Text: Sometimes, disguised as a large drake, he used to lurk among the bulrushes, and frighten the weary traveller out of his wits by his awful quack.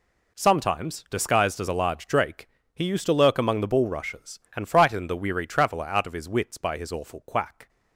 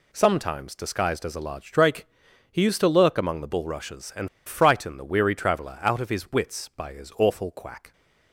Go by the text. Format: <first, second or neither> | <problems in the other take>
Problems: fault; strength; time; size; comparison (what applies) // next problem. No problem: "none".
first | pauses between "and" and "frighten"; slight; at 4.2 s; 0.17 s long